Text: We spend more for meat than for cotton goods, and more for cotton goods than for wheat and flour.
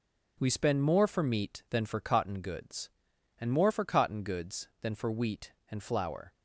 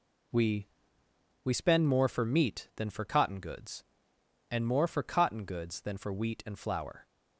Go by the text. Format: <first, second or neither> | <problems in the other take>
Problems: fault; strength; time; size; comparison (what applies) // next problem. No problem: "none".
first | says "We" twice; at 1.4 s